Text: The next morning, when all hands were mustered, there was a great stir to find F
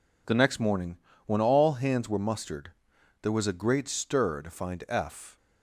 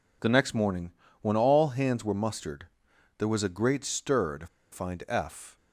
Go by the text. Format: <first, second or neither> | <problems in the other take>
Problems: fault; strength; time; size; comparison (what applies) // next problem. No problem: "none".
first | pauses between "to" and "find"; slight; at 4.4 s; 0.25 s long